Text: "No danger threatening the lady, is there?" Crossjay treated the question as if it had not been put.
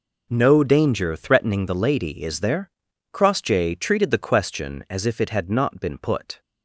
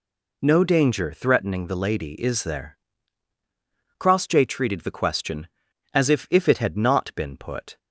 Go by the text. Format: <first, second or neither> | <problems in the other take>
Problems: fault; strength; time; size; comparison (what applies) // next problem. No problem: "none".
first | says "if" twice; at 6.2 s